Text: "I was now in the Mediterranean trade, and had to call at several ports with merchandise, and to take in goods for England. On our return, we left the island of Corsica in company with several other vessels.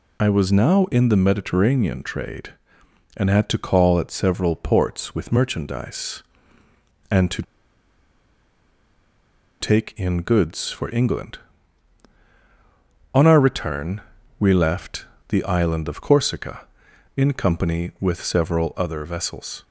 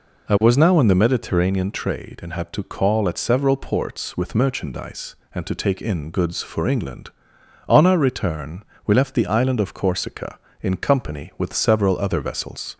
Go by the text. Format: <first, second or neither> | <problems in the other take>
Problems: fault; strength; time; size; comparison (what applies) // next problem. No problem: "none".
second | pauses between "to" and "take"; strong; at 7.4 s; 2.1 s long // pauses between "left" and "the"; slight; at 15.0 s; 0.24 s long